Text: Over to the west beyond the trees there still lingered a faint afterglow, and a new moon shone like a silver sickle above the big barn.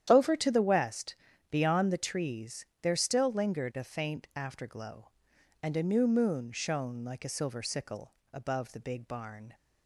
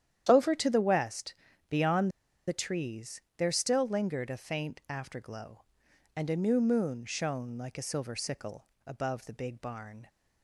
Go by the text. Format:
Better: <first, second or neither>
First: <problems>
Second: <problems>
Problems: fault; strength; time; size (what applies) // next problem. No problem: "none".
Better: first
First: starts louder than the rest; strong; until 1.1 s; 10 dB // pauses between "west" and "beyond"; slight; at 1.1 s; 0.36 s long // pauses between "trees" and "there"; slight; at 2.6 s; 0.16 s long // pauses between "sickle" and "above"; slight; at 8.1 s; 0.20 s long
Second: starts louder than the rest; strong; until 1.3 s; 10 dB // pauses between "west" and "beyond"; slight; at 1.3 s; 0.36 s long // pauses between "beyond" and "the"; at 2.1 s; 0.37 s long // pauses between "trees" and "there"; slight; at 3.2 s; 0.16 s long // pauses between "sickle" and "above"; slight; at 8.6 s; 0.20 s long